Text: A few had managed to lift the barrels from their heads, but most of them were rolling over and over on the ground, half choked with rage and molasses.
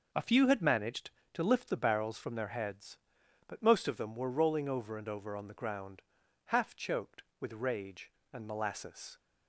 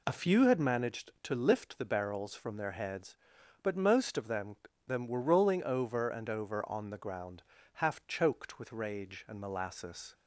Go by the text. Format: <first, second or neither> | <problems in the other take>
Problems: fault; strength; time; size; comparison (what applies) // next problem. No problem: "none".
first | says "them" twice; at 4.8 s